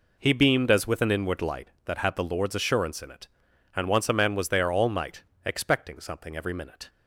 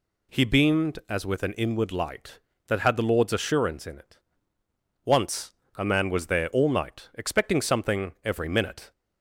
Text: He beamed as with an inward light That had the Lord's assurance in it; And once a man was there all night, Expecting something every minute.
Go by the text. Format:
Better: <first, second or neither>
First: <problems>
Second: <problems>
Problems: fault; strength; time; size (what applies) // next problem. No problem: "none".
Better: first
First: none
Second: skips "And"; at 4.6 s // pauses between "once" and "a"; slight; at 5.5 s; 0.22 s long